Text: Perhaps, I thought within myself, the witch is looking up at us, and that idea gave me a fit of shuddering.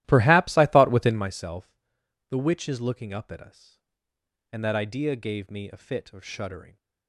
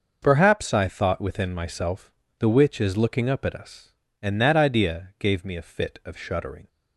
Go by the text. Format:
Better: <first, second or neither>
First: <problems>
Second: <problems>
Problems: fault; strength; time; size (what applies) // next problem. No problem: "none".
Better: second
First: starts louder than the rest; strong; until 1.3 s; 15 dB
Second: none